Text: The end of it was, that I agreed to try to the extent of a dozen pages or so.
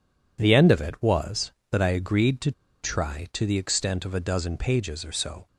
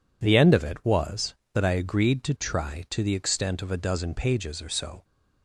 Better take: second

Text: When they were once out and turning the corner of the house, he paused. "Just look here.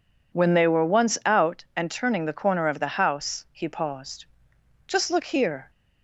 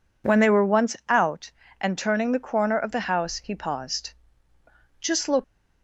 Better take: first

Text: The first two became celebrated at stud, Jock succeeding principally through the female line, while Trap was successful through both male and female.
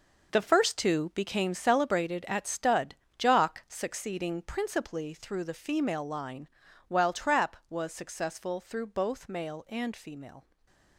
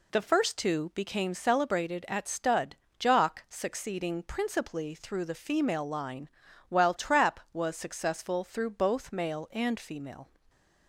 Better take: second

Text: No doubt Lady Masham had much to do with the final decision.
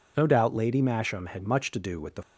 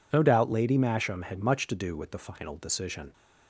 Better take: second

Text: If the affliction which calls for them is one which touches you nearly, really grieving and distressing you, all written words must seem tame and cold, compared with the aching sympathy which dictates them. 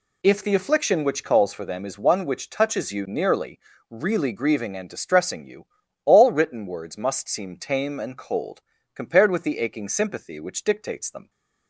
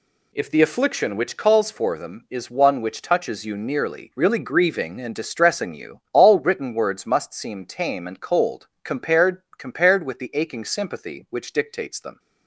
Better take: first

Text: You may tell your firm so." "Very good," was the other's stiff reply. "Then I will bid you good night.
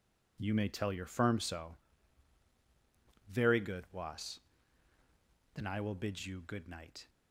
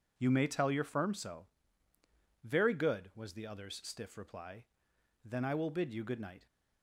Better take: second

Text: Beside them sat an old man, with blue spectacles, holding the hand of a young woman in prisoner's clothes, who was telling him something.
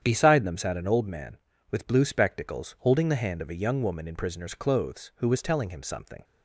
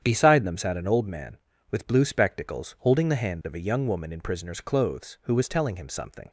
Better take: neither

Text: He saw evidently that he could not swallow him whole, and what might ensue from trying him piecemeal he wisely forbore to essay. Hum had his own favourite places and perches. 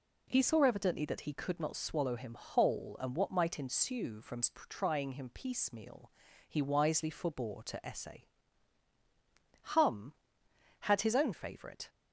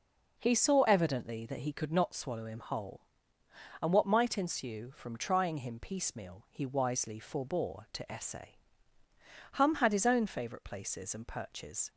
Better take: second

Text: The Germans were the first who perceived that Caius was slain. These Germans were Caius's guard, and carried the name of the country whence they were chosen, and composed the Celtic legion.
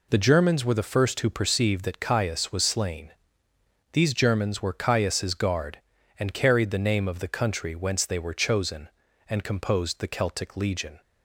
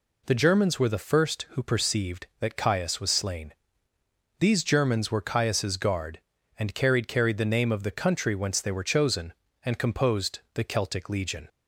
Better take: first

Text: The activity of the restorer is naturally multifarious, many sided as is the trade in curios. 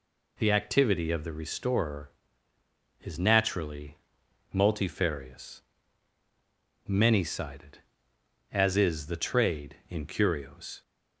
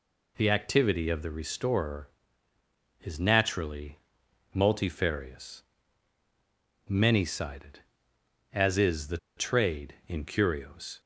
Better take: first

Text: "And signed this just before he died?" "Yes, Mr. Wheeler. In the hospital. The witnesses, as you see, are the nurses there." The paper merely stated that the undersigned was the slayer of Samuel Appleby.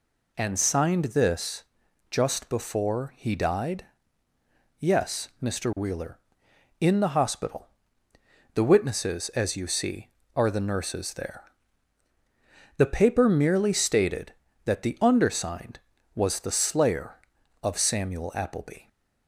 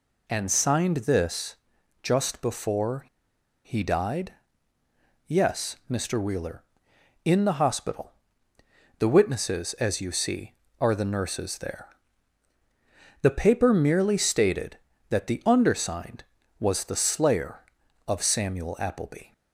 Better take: first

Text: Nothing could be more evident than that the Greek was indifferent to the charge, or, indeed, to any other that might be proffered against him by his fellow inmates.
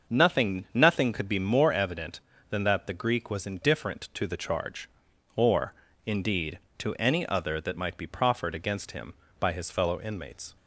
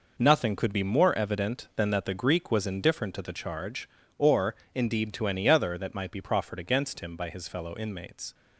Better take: second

